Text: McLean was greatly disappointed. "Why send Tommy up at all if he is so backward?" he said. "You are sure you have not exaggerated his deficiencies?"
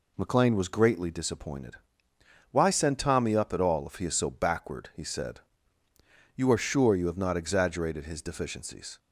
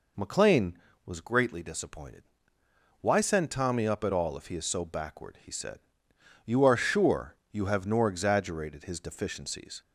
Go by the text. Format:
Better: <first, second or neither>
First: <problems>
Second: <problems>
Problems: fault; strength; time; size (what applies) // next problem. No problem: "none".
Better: first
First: none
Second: pauses between "sure" and "you"; slight; at 7.3 s; 0.16 s long // says "nor" for "not"; at 7.8 s